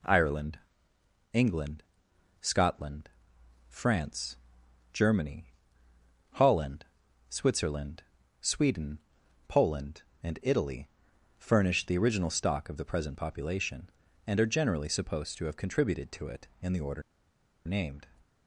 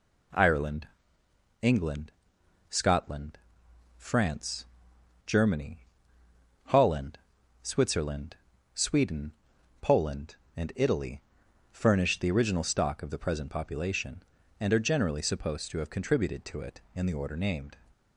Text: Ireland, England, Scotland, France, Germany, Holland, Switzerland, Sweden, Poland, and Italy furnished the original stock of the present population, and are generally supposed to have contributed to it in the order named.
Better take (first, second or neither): second